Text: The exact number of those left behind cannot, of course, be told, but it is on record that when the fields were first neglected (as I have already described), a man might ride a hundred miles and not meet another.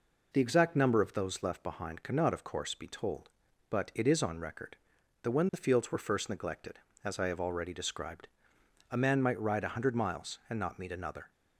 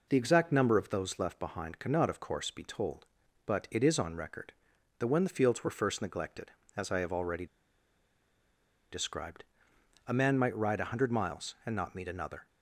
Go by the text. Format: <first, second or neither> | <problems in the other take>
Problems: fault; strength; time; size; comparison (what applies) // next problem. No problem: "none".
first | pauses between "already" and "described"; strong; at 7.4 s; 1.4 s long